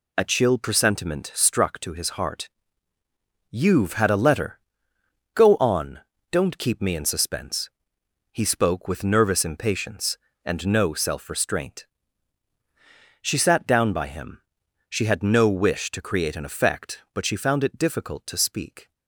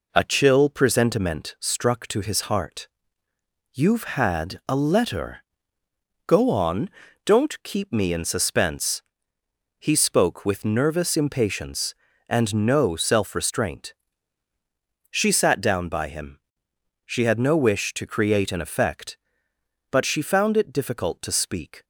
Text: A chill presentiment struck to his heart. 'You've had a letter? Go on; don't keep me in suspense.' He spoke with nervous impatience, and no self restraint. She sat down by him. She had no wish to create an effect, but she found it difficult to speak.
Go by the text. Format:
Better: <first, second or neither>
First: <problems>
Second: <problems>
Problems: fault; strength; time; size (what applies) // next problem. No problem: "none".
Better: neither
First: none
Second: none